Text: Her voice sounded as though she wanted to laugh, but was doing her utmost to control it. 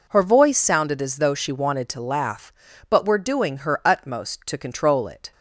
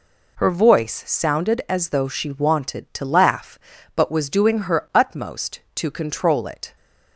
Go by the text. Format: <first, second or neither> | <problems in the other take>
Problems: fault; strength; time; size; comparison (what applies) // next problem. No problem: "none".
second | says "were" for "was"; at 3.0 s